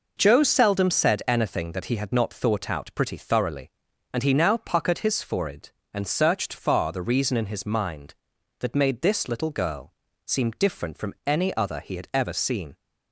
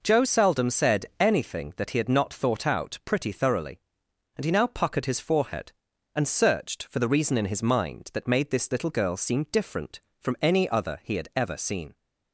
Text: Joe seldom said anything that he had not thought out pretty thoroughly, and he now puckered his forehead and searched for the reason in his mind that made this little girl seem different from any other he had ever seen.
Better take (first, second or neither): second